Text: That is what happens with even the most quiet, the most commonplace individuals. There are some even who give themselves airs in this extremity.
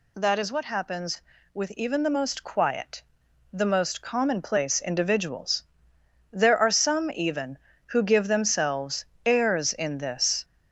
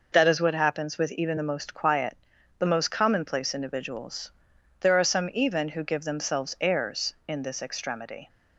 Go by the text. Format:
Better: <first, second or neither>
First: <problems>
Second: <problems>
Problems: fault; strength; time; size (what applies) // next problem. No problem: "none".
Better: second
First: pauses between "themselves" and "airs"; slight; at 9.0 s; 0.18 s long // stops before "extremity"; at 10.4 s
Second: none